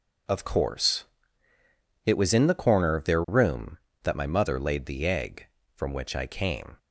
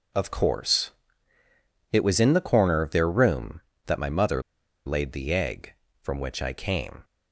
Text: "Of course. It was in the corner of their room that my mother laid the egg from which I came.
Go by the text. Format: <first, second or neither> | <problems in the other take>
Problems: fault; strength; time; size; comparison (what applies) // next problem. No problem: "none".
first | pauses between "mother" and "laid"; at 4.4 s; 0.44 s long